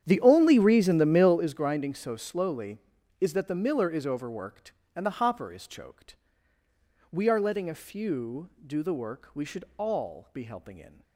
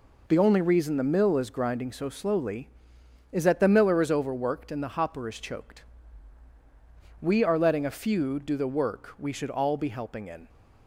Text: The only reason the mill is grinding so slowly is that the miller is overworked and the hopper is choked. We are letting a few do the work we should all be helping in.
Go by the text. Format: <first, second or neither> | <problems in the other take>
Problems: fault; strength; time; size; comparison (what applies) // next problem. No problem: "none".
second | starts louder than the rest; strong; until 1.6 s; 9 dB // pauses between "should" and "all"; slight; at 9.6 s; 0.16 s long